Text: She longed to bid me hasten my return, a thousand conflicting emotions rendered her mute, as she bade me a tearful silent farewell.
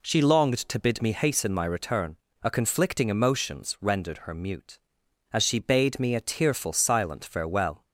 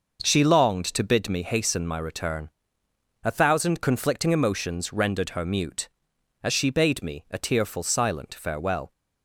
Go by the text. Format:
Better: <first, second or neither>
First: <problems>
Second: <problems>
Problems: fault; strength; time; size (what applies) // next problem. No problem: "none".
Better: second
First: skips "thousand"; at 2.5 s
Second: none